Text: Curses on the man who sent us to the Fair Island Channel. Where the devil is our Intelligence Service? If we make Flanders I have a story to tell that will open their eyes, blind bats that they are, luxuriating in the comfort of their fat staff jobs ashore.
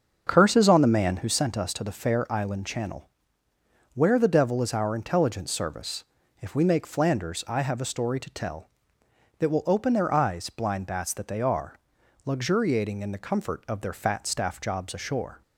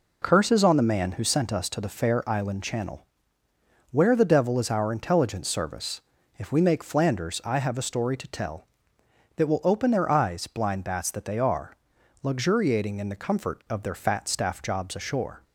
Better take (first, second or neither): second